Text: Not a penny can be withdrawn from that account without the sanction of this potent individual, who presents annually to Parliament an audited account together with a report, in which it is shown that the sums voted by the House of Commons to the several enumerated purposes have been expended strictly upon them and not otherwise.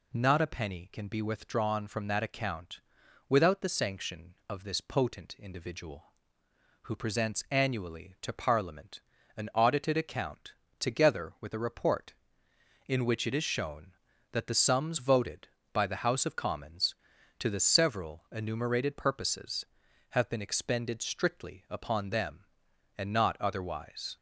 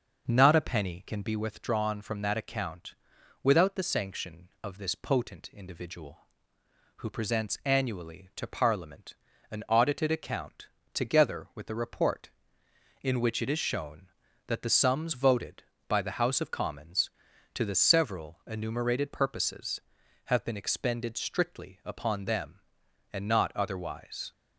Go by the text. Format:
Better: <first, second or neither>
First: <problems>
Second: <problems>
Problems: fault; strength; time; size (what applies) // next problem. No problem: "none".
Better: first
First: pauses between "account" and "without"; noticeable; at 2.8 s; 0.50 s long // pauses between "Parliament" and "an"; at 9.0 s; 0.38 s long // pauses between "account" and "together"; slight; at 10.5 s; 0.26 s long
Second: starts louder than the rest; noticeable; until 1.4 s; 6 dB // pauses between "account" and "without"; noticeable; at 2.9 s; 0.50 s long // pauses between "Parliament" and "an"; at 9.1 s; 0.38 s long // pauses between "account" and "together"; slight; at 10.6 s; 0.26 s long